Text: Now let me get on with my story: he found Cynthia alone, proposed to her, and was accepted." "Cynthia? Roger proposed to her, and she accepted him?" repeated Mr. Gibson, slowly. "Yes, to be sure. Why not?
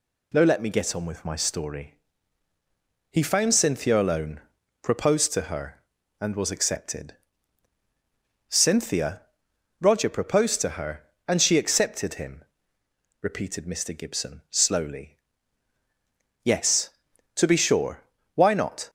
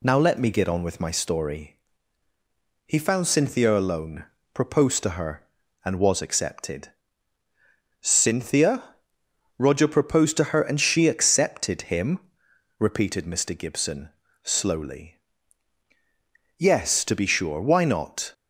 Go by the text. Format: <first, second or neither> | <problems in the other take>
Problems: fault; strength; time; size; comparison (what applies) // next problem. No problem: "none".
neither | none